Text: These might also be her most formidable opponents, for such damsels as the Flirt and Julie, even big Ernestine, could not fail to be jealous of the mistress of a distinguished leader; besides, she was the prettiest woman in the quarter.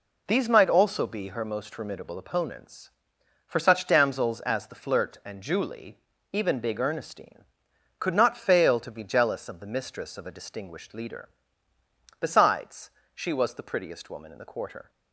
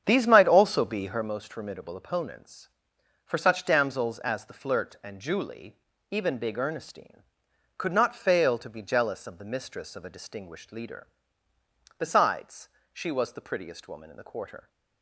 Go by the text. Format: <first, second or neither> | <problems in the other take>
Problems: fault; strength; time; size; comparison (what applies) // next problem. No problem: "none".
first | starts louder than the rest; strong; until 1.4 s; 8 dB